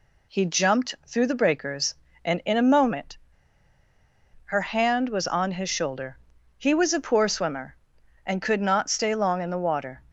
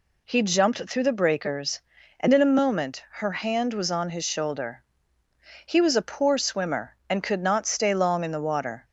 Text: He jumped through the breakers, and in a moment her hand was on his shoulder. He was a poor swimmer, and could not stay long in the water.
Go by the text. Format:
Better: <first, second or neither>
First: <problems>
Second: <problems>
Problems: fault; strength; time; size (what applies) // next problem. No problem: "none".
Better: second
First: pauses between "moment" and "her"; strong; at 3.1 s; 1.2 s long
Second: none